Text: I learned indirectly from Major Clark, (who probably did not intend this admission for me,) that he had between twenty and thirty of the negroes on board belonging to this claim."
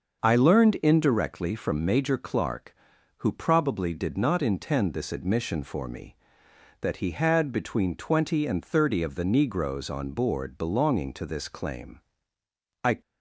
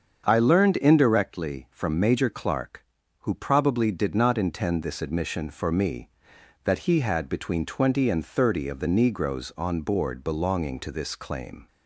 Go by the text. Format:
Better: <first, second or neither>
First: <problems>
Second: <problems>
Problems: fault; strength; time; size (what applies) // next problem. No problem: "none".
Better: second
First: starts louder than the rest; until 1.2 s; 6.5 dB // goes on to say "I"; slight; from 12.8 s on; 0.16 s long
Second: starts louder than the rest; until 1.2 s; 7 dB